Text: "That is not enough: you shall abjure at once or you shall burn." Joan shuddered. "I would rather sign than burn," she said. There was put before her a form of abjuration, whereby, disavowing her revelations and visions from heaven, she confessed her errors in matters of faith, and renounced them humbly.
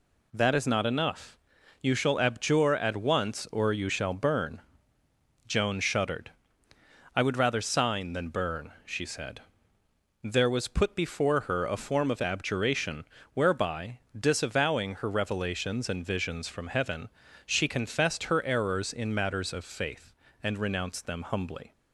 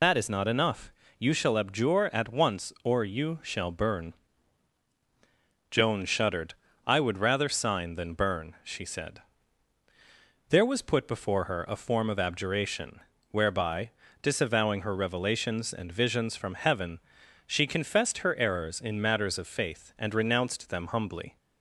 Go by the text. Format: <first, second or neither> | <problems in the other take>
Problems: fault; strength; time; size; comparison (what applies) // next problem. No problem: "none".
first | loses the start of "That"; at 0.0 s; 115 ms